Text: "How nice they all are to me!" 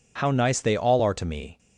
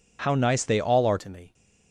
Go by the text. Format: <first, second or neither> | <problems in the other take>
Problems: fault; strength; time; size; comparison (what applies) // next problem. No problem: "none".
first | changes voice at "to"; from 1.1 s on; 0.4 s long